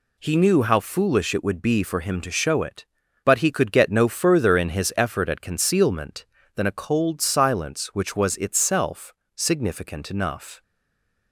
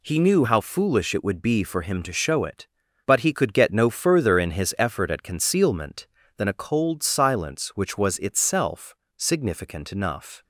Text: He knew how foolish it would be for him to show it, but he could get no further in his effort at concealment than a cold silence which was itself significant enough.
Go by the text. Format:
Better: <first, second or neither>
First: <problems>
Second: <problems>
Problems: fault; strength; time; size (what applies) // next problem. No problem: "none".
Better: second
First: pauses between "itself" and "significant"; slight; at 9.1 s; 0.24 s long // stays silent after the last word; slight; from 10.6 s on; 0.7 s long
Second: pauses between "itself" and "significant"; slight; at 8.9 s; 0.24 s long